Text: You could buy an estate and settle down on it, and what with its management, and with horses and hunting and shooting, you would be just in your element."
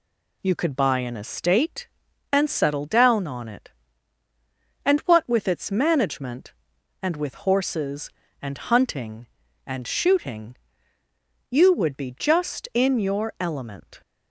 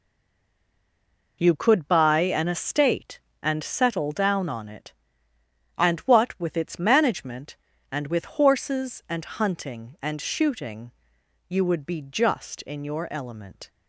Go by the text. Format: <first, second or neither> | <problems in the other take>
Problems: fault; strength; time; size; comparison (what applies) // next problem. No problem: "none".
first | stays silent before the first word; noticeable; until 1.4 s; 1.4 s long